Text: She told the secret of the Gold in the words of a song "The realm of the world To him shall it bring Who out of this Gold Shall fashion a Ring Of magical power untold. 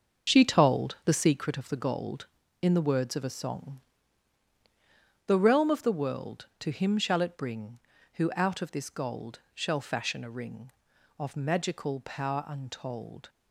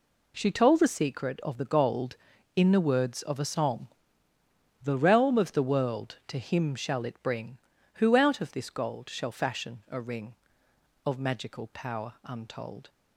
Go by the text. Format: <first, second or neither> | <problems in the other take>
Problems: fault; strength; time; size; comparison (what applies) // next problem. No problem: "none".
second | starts louder than the rest; until 1.5 s; 6.5 dB // pauses between "song" and "The"; strong; at 3.8 s; 1.4 s long; noticeable in the second // pauses between "Gold" and "Shall"; slight; at 9.3 s; 0.16 s long